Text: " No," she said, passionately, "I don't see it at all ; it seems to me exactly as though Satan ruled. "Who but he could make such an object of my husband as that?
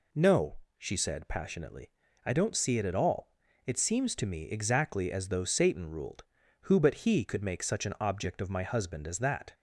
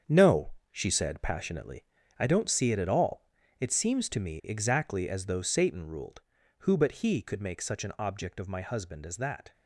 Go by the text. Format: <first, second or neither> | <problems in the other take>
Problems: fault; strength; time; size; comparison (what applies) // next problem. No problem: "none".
first | gets quieter; strong; throughout; 7.5 dB